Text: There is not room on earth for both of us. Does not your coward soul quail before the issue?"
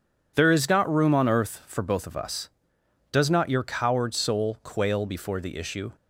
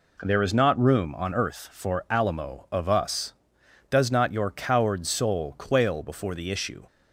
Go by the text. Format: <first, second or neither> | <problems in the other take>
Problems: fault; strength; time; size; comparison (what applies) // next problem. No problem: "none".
first | says "alamo" for "both"; at 2.0 s